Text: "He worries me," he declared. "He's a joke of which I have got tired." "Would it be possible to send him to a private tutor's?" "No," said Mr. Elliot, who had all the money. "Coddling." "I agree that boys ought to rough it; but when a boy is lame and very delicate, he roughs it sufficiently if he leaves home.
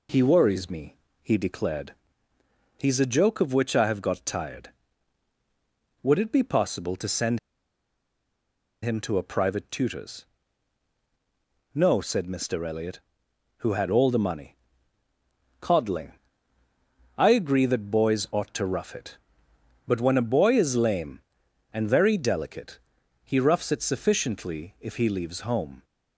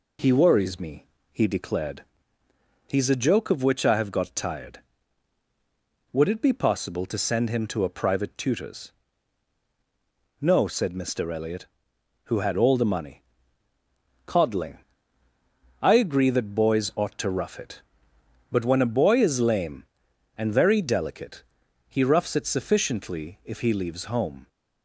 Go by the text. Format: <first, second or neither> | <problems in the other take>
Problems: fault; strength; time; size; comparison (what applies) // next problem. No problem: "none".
second | pauses between "send" and "him"; strong; at 7.3 s; 1.4 s long